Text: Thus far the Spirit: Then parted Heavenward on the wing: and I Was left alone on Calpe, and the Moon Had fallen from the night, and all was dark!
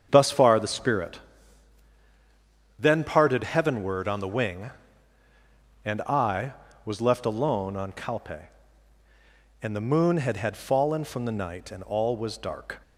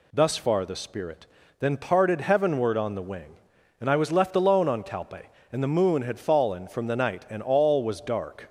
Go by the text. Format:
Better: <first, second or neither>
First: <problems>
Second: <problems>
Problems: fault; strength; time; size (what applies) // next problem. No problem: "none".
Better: second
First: starts louder than the rest; strong; until 1.1 s; 7.5 dB // says "Had" twice; at 10.3 s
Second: none